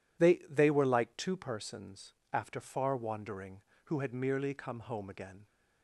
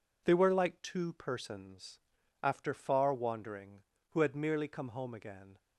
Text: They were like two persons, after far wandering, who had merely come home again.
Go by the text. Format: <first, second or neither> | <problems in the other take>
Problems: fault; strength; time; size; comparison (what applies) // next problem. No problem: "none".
second | says "They" twice; at 0.4 s